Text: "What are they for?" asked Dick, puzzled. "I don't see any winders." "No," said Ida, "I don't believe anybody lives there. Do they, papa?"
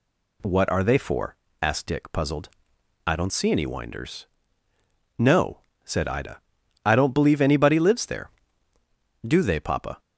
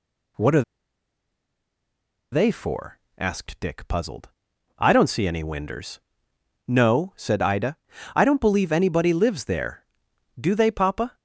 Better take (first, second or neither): first